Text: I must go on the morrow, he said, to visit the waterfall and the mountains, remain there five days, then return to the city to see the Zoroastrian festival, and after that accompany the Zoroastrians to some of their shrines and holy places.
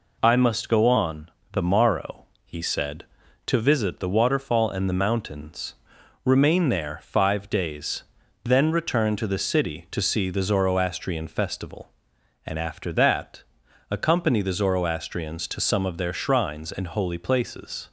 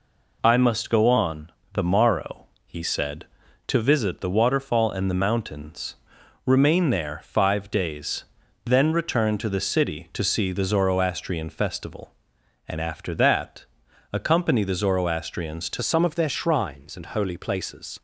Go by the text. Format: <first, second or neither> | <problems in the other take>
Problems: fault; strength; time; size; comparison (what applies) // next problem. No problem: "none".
first | pauses between "on" and "the"; slight; at 1.5 s; 0.22 s long; slight in the first // pauses between "that" and "accompany"; noticeable; at 13.6 s; 0.48 s long; noticeable in the first // changes voice at "some"; from 15.8 s on; 2.2 s long